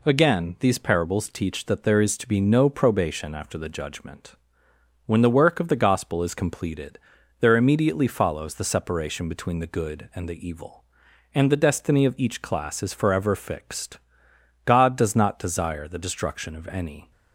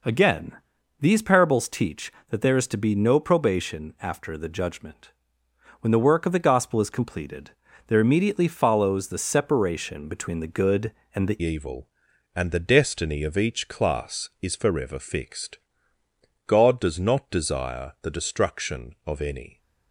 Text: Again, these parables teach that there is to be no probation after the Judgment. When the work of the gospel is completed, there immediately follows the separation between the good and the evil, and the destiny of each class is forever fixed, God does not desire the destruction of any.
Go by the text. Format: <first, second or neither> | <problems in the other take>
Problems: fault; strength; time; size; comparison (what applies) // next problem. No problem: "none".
first | changes voice at "evil"; from 11.3 s on; 8.2 s long